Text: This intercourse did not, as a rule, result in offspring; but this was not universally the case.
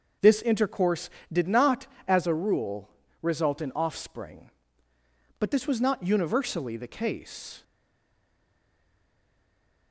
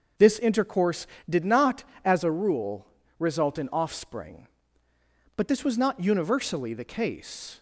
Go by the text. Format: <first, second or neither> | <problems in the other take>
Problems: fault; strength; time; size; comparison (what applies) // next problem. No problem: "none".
second | starts louder than the rest; until 1.4 s; 6.5 dB; also in the second // stays silent after the last word; from 7.6 s on; 2.3 s long